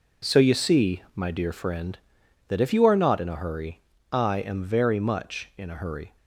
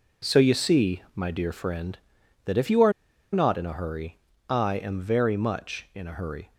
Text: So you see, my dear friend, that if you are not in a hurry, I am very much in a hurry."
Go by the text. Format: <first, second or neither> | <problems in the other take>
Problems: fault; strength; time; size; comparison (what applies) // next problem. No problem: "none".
first | pauses between "are" and "not"; at 2.9 s; 0.41 s long